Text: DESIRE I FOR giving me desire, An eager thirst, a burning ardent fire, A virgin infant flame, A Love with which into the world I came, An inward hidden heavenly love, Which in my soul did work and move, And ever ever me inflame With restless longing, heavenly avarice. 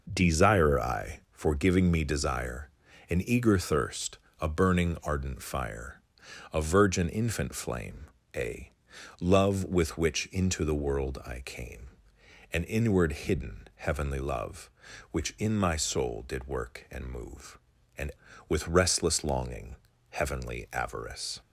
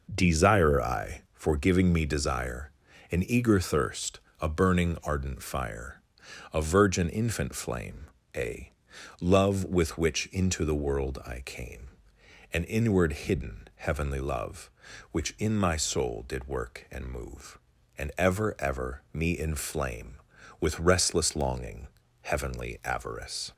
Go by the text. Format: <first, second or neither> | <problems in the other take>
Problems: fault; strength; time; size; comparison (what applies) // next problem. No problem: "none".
second | pauses between "A" and "Love"; noticeable; at 8.7 s; 0.48 s long; noticeable in the second // skips "ever ever me inflame"; at 18.3 s